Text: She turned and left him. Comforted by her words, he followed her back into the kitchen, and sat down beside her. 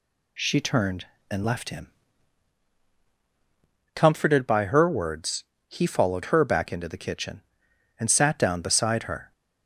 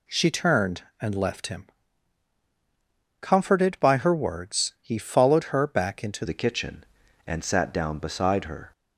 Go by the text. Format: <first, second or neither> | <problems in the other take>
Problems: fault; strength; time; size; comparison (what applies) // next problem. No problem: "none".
first | changes voice at "the"; from 6.2 s on; 2.5 s long